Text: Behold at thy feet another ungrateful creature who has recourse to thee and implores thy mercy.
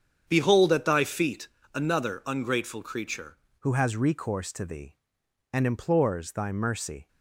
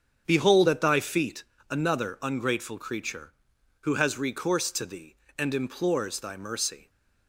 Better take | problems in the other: second | starts louder than the rest; strong; until 1.2 s; 8 dB; strong in the second // pauses between "feet" and "another"; slight; at 1.4 s; 0.26 s long; slight in the second // changes voice at "who"; from 3.5 s on; 3.5 s long

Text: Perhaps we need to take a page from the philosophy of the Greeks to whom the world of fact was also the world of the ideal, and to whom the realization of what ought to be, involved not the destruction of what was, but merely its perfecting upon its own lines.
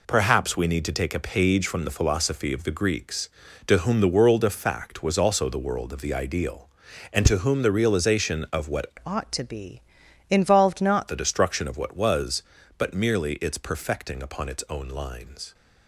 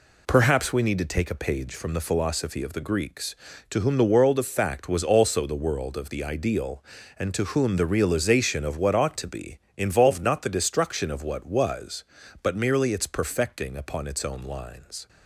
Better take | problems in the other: second | changes voice from "ought" to "not"; from 9.0 to 11.0 s; 2.0 s long

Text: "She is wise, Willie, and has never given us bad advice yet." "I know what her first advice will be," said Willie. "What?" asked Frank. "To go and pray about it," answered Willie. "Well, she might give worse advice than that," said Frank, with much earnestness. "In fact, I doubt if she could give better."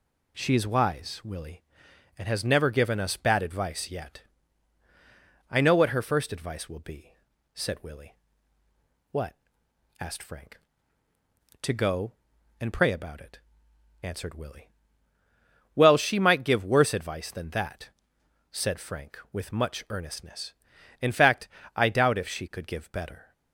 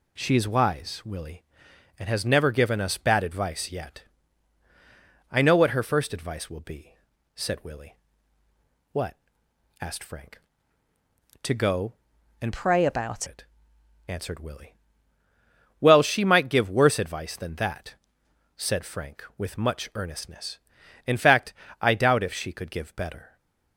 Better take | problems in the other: first | changes voice from "pray" to "about"; from 12.5 to 13.2 s; 0.7 s long // stays silent after the last word; slight; from 23.2 s on; 0.5 s long

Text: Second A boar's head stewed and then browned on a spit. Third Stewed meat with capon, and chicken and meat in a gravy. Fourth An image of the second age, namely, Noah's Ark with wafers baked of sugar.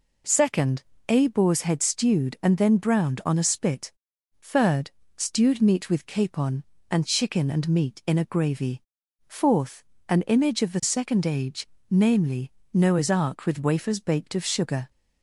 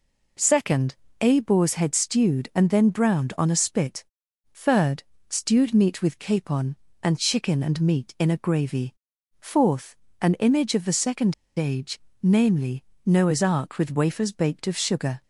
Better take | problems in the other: first | pauses between "Second" and "A"; slight; at 0.9 s; 0.26 s long; slight in the first // pauses between "Third" and "Stewed"; slight; at 5.0 s; 0.28 s long; slight in the first // pauses between "Fourth" and "An"; slight; at 9.9 s; 0.26 s long; slight in the first // pauses between "second" and "age"; slight; at 11.3 s; 0.24 s long

